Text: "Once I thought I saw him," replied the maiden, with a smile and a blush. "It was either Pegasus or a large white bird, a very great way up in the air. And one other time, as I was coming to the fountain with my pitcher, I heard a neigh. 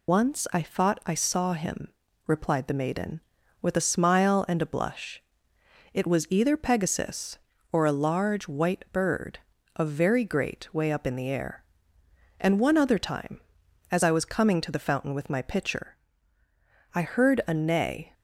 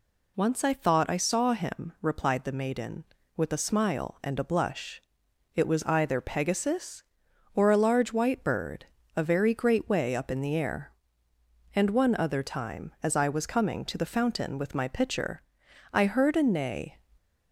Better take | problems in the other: second | loses the start of "Once"; at 0.0 s; 60 ms

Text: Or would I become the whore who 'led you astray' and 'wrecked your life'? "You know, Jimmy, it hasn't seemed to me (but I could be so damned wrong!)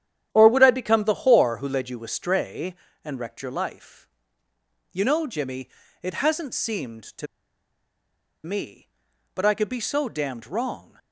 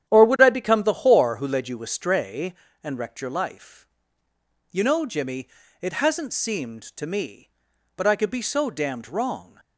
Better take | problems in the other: second | starts louder than the rest; strong; until 1.3 s; 10 dB; strong in the second // pauses between "to" and "me"; at 7.2 s; 1.1 s long

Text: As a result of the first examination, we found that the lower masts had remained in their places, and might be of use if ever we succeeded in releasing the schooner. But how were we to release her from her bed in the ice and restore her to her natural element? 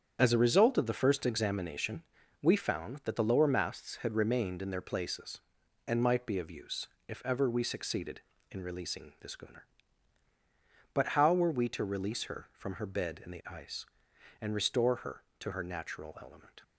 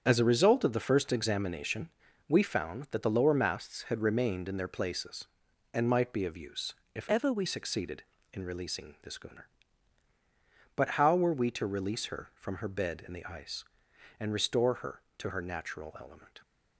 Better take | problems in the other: first | starts louder than the rest; strong; until 1.0 s; 7.5 dB; strong in the first // pauses between "use" and "if"; slight; at 6.7 s; 0.20 s long; slight in the first // changes voice from "ever" to "we"; from 7.0 to 7.4 s; 0.4 s long

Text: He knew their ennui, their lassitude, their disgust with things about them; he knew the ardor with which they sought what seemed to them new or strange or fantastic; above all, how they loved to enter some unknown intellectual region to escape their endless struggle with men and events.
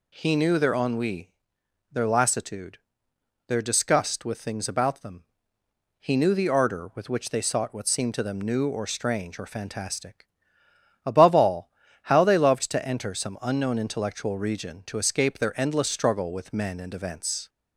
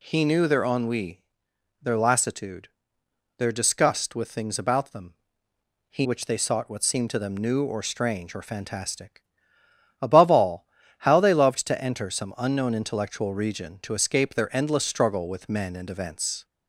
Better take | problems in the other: first | skips "knew the ardor with"; at 6.0 s

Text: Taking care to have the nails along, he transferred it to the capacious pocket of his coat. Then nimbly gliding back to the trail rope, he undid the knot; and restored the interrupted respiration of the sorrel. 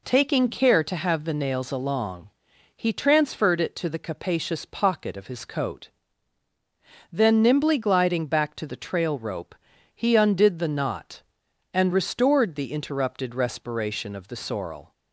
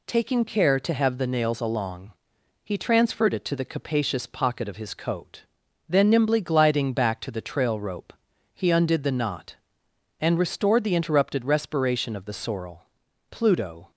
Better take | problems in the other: first | goes on to say "Pluto"; from 13.3 s on; 0.60 s long

